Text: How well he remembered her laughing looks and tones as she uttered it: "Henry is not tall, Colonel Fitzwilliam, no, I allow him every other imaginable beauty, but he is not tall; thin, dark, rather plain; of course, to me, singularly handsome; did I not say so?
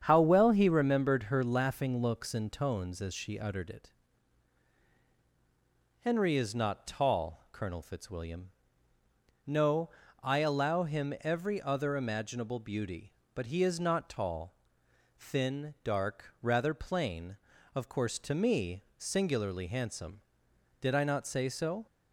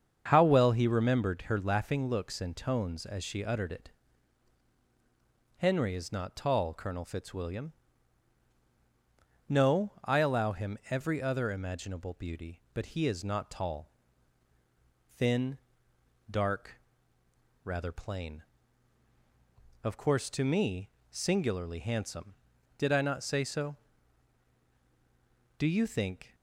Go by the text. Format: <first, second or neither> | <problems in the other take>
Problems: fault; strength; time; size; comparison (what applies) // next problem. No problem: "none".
first | starts louder than the rest; strong; until 1.3 s; 7 dB; strong in the first // goes on to say "Do you think"; noticeable; from 25.5 s on; 0.78 s long